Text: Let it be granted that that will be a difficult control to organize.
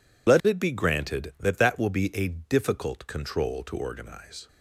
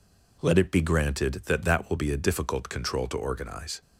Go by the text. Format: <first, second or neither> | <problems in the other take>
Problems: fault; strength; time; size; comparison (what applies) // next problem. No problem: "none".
second | loses the start of "Let"; at 0.2 s; 35 ms